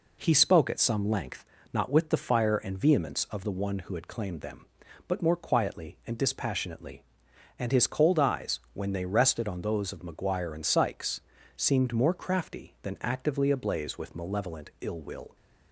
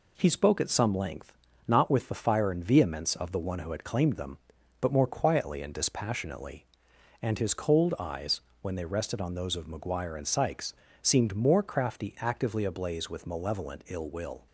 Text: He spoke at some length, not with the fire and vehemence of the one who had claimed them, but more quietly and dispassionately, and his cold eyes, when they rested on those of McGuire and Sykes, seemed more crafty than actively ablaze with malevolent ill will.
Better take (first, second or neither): first